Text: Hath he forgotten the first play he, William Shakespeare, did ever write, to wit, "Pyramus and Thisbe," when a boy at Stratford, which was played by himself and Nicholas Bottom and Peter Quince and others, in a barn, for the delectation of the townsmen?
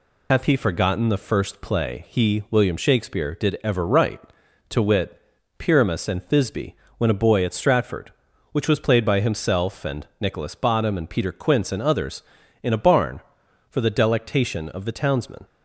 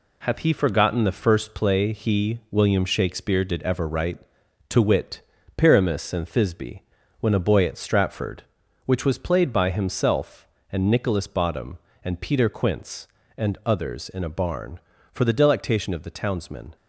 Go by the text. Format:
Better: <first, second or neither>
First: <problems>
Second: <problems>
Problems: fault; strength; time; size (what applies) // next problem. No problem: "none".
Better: second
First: loses the start of "Hath"; at 0.3 s; 80 ms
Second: none